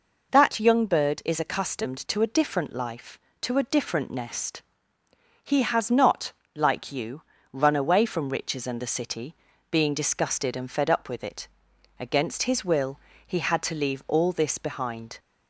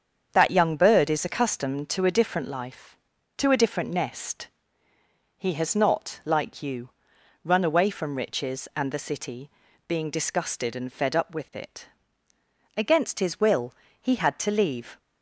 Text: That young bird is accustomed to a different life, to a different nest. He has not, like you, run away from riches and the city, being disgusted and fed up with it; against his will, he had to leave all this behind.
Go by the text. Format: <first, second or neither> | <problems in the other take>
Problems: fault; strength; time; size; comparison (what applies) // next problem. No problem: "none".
first | starts louder than the rest; strong; until 1.3 s; 7 dB // stops before "all this behind"; at 14.9 s